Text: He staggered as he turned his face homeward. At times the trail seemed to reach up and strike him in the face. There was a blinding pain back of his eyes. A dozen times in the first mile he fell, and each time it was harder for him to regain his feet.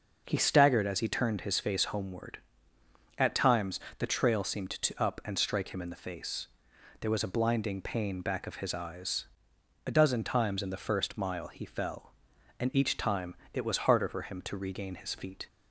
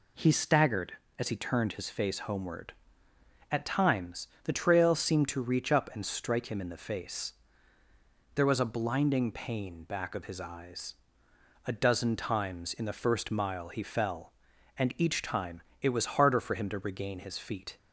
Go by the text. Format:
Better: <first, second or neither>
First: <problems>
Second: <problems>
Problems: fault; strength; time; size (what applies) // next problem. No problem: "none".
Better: second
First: pauses between "times" and "the"; slight; at 3.7 s; 0.20 s long // skips "reach"; at 5.0 s // pauses between "time" and "it"; slight; at 13.3 s; 0.18 s long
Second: pauses between "times" and "the"; slight; at 4.2 s; 0.16 s long // pauses between "time" and "it"; slight; at 15.6 s; 0.20 s long